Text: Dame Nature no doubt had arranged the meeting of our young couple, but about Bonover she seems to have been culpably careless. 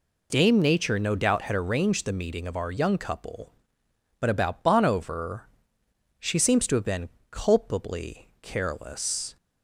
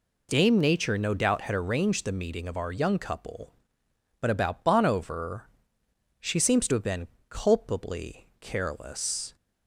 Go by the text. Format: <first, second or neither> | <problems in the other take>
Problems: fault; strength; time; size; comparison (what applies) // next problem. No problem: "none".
neither | pauses between "Bonover" and "she"; noticeable; the same in both // pauses between "been" and "culpably"; slight; the same in both